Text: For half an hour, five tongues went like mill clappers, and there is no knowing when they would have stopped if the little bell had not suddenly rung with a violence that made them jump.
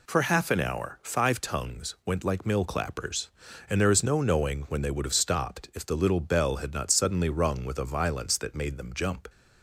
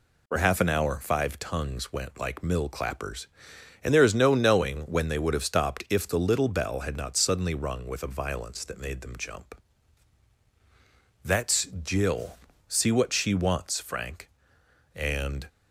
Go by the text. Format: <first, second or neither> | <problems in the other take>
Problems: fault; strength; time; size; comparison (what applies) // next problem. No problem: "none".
first | goes on to say "That's Jill see what she wants Frank and"; strong; from 11.2 s on; 4.2 s long